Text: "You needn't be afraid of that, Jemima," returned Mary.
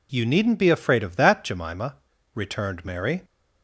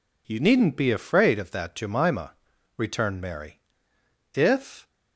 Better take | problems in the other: first | goes on to say "If"; from 4.3 s on; 0.54 s long

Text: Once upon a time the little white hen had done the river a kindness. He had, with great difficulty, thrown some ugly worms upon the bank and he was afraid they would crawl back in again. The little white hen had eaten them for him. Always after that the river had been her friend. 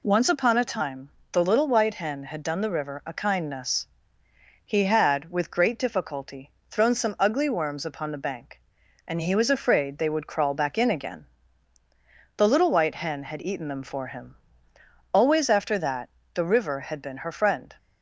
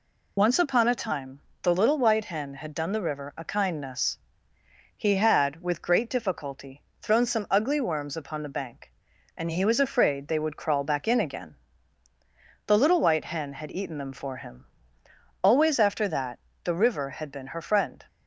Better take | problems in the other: first | loses the start of "Once"; at 0.3 s; 45 ms // pauses between "time" and "the"; slight; at 1.3 s; 0.22 s long; slight in the first // pauses between "that" and "the"; slight; at 16.3 s; 0.24 s long; slight in the first

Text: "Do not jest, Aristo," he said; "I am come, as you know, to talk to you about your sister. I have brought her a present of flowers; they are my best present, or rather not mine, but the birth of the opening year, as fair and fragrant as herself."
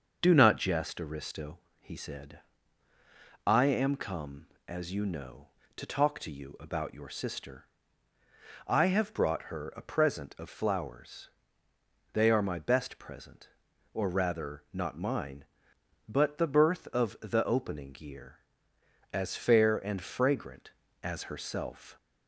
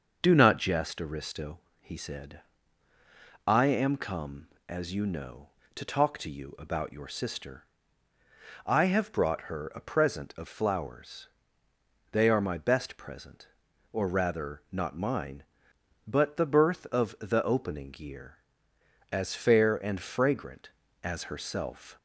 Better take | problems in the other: neither | starts louder than the rest; the same in both

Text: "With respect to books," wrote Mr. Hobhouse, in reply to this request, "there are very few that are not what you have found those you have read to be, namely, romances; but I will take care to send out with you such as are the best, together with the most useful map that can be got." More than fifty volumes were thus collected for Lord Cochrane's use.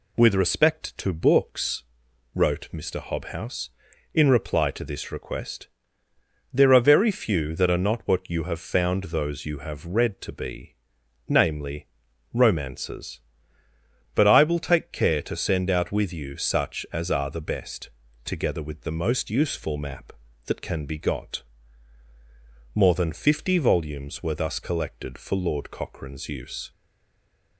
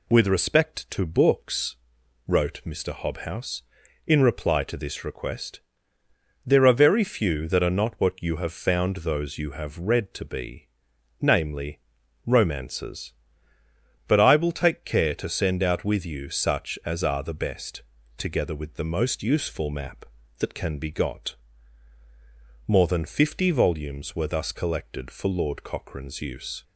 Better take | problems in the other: second | stays silent after the last word; slight; from 26.7 s on; 0.8 s long

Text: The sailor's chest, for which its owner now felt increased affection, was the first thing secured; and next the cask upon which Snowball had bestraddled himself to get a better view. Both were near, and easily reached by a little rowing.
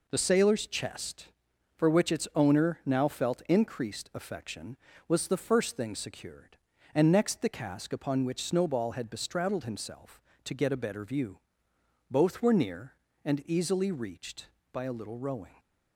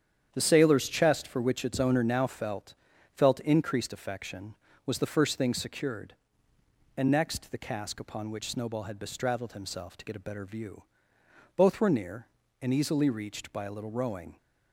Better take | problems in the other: first | starts louder than the rest; strong; until 1.3 s; 9 dB // says "felt" twice; at 3.1 s

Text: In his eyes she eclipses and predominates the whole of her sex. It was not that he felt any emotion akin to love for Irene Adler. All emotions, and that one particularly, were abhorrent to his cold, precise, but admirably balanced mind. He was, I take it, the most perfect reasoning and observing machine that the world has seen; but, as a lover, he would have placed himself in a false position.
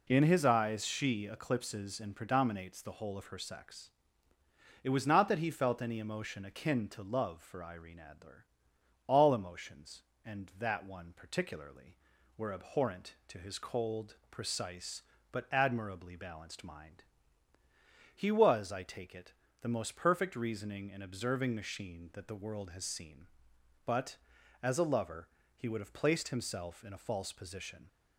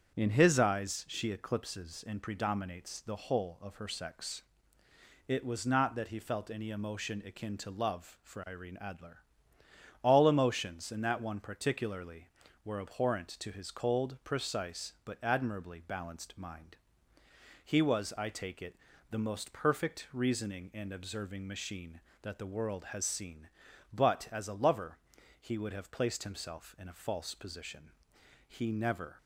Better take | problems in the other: first | starts louder than the rest; strong; until 1.1 s; 8 dB // goes on to say "He never"; noticeable; from 28.4 s on; 0.70 s long

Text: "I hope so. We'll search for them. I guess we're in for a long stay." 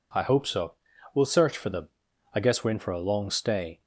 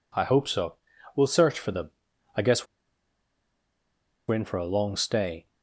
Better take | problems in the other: first | pauses between "guess" and "we're"; strong; at 2.6 s; 1.6 s long

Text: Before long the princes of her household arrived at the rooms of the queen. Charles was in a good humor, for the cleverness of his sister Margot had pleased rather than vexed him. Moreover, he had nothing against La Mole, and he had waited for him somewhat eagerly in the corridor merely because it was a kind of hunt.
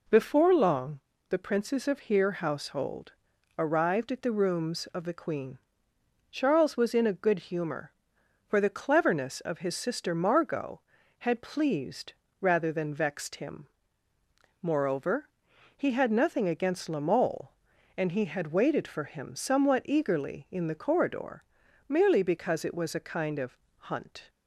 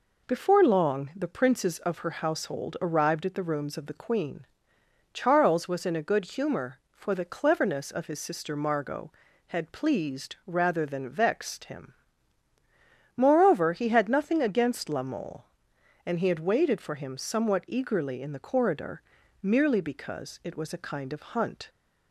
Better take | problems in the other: second | pauses between "long" and "the"; slight; at 1.0 s; 0.26 s long // says "here" for "her"; at 1.9 s // pauses between "household" and "arrived"; noticeable; at 3.1 s; 0.46 s long // pauses between "pleased" and "rather"; slight; at 12.1 s; 0.26 s long // pauses between "corridor" and "merely"; noticeable; at 21.4 s; 0.46 s long; also in the second // pauses between "of" and "hunt"; slight; at 23.5 s; 0.20 s long

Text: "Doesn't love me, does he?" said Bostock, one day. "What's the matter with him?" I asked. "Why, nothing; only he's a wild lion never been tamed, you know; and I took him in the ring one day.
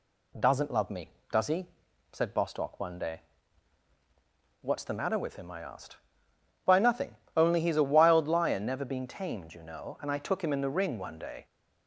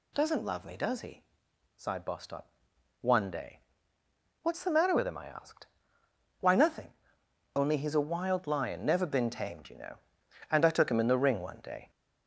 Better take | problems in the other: first | says "sighed" for "said"; at 1.7 s

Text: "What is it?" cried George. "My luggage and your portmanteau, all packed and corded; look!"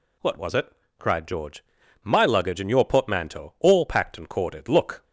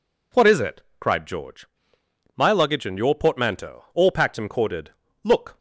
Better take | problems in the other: second | says "was" for "is"; at 0.3 s

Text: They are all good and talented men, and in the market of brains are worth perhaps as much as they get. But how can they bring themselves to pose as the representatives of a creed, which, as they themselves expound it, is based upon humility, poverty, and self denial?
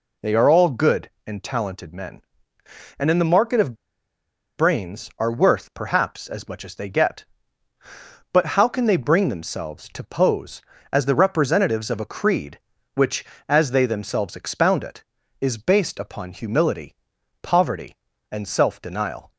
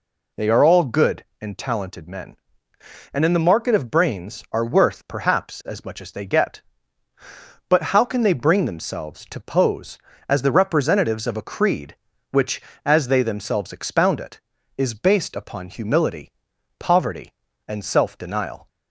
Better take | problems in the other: second | pauses between "of" and "brains"; noticeable; at 3.7 s; 0.81 s long

